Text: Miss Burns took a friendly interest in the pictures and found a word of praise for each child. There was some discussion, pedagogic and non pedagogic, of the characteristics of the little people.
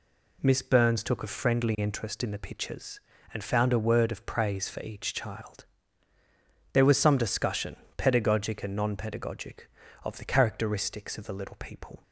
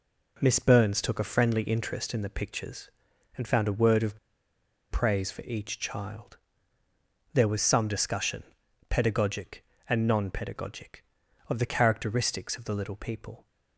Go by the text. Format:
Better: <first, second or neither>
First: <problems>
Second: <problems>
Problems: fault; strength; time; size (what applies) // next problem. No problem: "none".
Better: first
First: none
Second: pauses between "of" and "praise"; noticeable; at 4.1 s; 0.72 s long